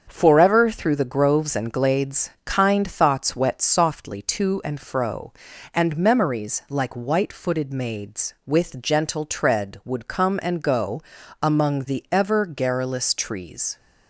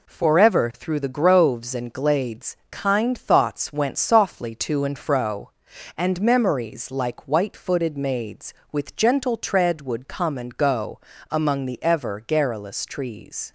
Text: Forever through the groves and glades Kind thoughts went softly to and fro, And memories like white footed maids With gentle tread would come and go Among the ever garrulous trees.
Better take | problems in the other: second | starts louder than the rest; until 1.0 s; 7 dB // pauses between "glades" and "Kind"; slight; at 2.3 s; 0.16 s long // says "wet" for "went"; at 3.3 s // pauses between "go" and "Among"; at 11.0 s; 0.40 s long; slight in the second

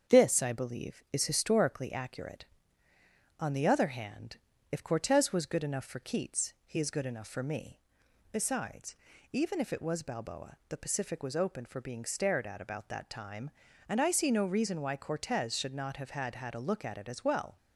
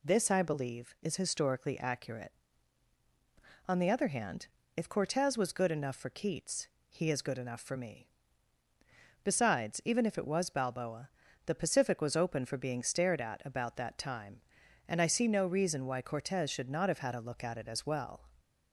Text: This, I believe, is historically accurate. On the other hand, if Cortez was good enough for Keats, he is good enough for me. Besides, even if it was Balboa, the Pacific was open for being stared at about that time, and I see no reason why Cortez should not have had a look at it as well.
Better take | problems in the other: second | starts louder than the rest; strong; until 1.2 s; 7.5 dB // says "had" twice; at 16.3 s

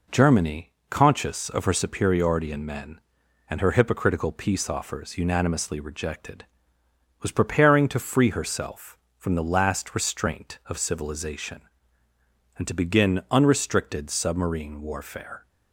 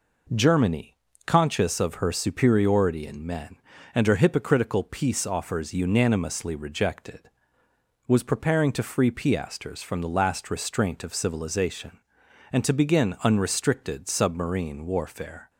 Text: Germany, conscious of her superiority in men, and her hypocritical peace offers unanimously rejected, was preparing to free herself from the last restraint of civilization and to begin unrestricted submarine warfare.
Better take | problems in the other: first | says "piasters" for "herself"; at 9.0 s

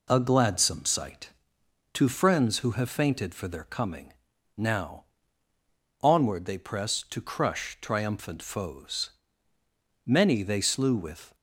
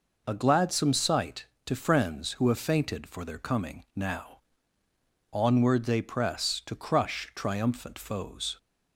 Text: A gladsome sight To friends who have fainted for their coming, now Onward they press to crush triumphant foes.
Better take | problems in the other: second | pauses between "now" and "Onward"; noticeable; at 5.0 s; 0.96 s long; noticeable in the second // goes on to say "Many they slew with"; noticeable; from 10.0 s on; 1.2 s long

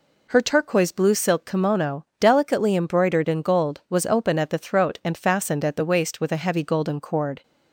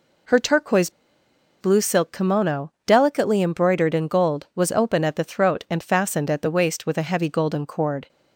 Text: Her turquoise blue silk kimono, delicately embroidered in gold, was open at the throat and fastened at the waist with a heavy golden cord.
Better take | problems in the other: first | pauses between "turquoise" and "blue"; noticeable; at 0.8 s; 0.70 s long

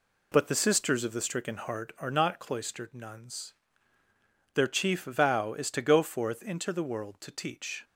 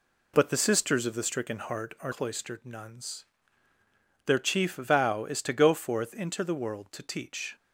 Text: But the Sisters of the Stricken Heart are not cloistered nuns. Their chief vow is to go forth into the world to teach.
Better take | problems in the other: first | skips "not"; at 2.1 s

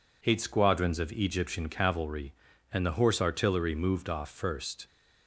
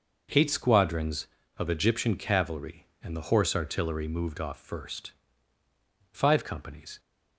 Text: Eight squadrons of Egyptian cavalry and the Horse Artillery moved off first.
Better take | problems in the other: first | goes on to say "Five companies"; noticeable; from 6.1 s on; 0.88 s long

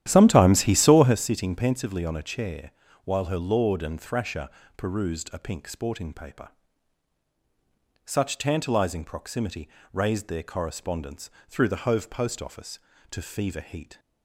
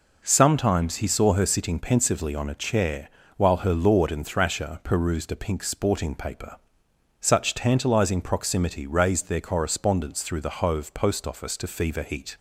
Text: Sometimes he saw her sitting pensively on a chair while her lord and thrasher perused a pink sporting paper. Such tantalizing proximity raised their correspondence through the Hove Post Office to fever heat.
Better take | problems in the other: second | starts louder than the rest; strong; until 1.2 s; 11.5 dB // pauses between "chair" and "while"; slight; at 2.7 s; 0.32 s long; slight in the second // pauses between "thrasher" and "perused"; slight; at 4.4 s; 0.30 s long // pauses between "proximity" and "raised"; slight; at 9.6 s; 0.24 s long // pauses between "correspondence" and "through"; slight; at 11.2 s; 0.20 s long

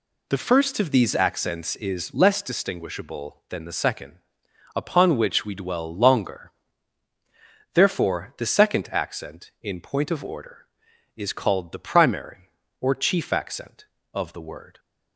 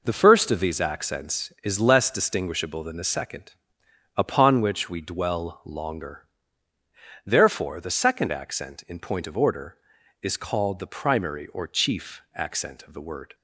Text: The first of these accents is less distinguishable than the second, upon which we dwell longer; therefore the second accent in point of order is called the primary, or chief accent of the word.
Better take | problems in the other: neither | none

